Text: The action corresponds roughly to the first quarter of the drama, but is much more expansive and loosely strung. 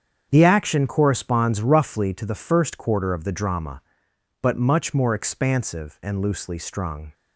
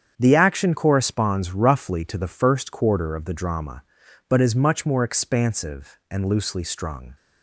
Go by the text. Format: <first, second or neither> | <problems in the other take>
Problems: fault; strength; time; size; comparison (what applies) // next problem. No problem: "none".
second | starts louder than the rest; strong; until 1.3 s; 7.5 dB; strong in the second // skips "is"; at 4.5 s